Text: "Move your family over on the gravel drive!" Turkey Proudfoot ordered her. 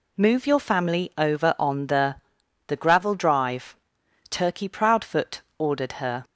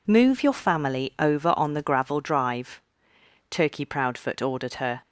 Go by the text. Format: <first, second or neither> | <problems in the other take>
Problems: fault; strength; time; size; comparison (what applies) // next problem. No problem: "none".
second | says "the" twice; at 2.6 s // pauses between "Proudfoot" and "ordered"; slight; at 5.3 s; 0.18 s long